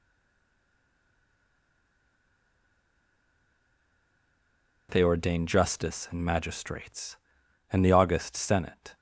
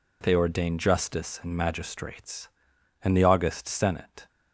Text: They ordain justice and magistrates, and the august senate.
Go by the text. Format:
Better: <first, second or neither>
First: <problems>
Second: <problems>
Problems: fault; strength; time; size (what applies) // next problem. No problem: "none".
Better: second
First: stays silent before the first word; strong; until 4.8 s; 4.8 s long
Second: none